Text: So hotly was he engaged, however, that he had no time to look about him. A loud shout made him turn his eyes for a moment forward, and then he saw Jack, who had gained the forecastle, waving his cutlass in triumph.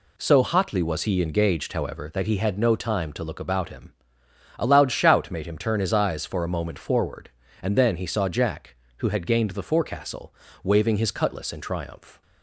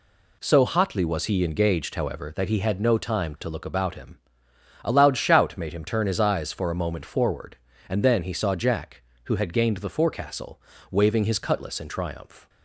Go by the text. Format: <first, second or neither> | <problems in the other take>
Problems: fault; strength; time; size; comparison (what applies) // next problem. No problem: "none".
neither | none